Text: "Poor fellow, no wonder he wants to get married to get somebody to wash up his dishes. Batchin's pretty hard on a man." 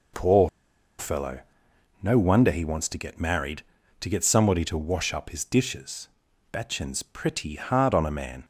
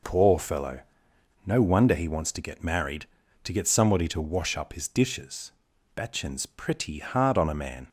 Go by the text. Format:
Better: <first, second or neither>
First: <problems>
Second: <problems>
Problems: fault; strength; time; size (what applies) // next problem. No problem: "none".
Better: second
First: pauses between "Poor" and "fellow"; noticeable; at 0.4 s; 0.50 s long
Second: none